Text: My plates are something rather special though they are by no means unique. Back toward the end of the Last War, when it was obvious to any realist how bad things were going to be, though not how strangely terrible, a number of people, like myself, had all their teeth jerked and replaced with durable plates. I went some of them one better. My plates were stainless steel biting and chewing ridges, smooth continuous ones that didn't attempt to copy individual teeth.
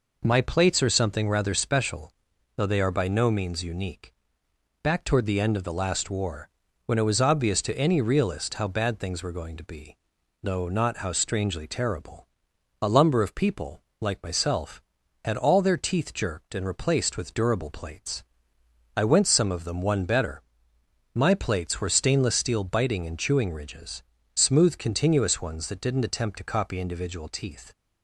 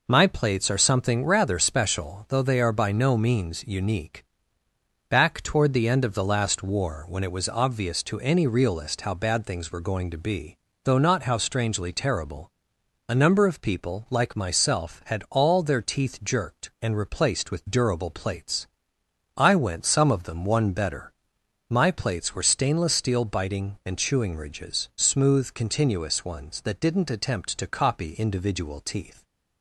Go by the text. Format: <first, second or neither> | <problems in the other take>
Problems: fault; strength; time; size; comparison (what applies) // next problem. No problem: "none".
second | pauses between "special" and "though"; noticeable; at 2.0 s; 0.46 s long // says "lumber" for "number"; at 12.8 s